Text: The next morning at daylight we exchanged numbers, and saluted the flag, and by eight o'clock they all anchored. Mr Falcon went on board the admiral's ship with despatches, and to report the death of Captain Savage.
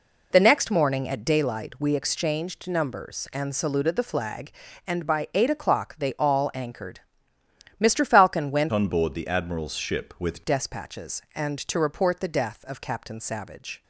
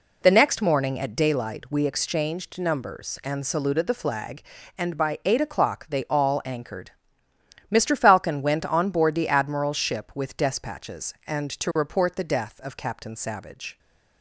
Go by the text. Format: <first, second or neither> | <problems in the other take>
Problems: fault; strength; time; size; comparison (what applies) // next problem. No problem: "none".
second | changes voice from "on" to "with"; from 8.7 to 10.4 s; 1.7 s long